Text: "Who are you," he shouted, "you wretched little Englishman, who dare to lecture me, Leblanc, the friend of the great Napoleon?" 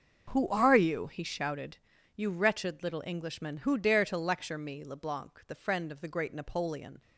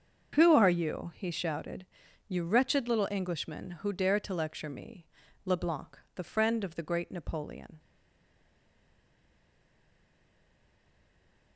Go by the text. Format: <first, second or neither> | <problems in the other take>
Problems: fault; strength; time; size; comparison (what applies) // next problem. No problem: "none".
first | starts louder than the rest; until 1.3 s; 6.5 dB; also in the first // stays silent after the last word; strong; from 7.7 s on; 3.8 s long